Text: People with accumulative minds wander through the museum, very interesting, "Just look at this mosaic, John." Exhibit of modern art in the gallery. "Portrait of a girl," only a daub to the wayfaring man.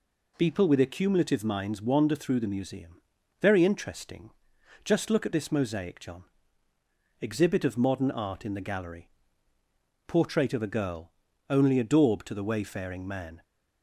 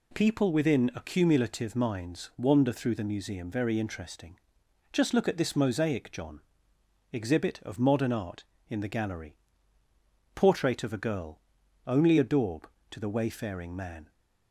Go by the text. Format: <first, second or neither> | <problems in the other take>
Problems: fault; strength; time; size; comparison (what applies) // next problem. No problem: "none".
first | says "within" for "with"; at 0.5 s